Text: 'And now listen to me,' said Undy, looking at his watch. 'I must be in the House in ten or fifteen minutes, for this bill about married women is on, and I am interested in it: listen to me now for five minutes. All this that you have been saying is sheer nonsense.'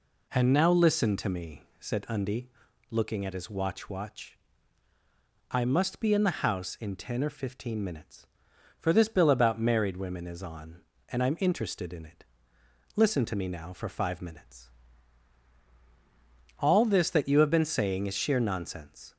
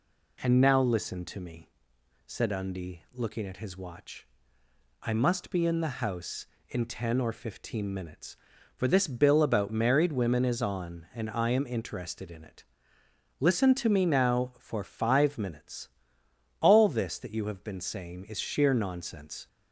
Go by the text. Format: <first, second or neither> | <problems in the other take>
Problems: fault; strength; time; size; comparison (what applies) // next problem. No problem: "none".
second | says "watch" twice; at 3.8 s